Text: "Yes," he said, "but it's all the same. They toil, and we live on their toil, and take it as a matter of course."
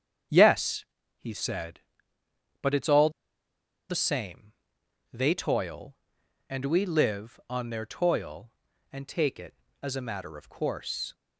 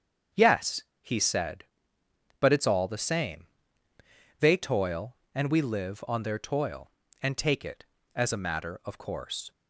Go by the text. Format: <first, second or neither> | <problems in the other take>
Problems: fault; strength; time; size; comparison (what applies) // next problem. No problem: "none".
second | starts louder than the rest; strong; until 1.6 s; 8 dB; strong in the second // pauses between "all" and "the"; noticeable; at 3.1 s; 0.78 s long